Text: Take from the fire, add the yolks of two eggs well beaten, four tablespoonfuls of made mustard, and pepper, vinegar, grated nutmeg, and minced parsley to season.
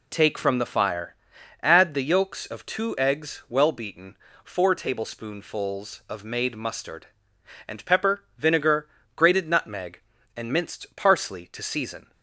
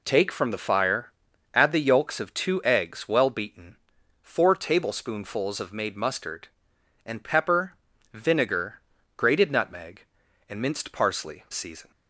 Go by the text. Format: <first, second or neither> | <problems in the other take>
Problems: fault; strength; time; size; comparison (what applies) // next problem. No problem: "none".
first | skips "to"; at 11.4 s